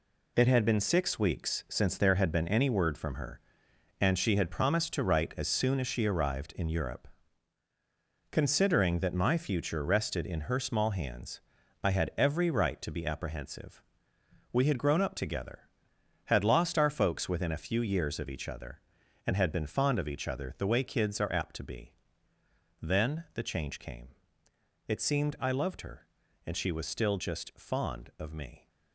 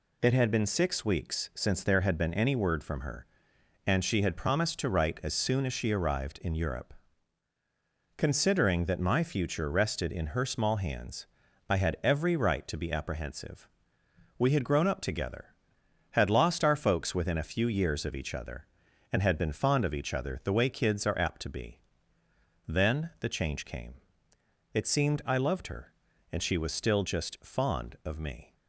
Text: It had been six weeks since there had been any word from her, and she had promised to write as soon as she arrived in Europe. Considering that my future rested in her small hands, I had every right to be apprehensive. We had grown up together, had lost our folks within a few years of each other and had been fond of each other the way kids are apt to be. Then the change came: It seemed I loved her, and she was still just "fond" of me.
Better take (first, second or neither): second